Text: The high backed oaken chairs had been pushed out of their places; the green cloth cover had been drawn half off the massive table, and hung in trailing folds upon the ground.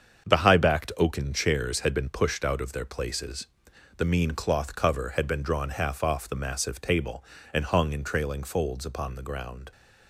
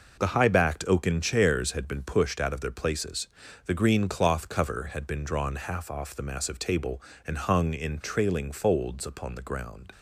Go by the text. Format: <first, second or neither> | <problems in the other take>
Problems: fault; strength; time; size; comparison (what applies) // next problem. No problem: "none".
second | starts louder than the rest; strong; until 1.3 s; 7.5 dB // says "mean" for "green"; at 4.0 s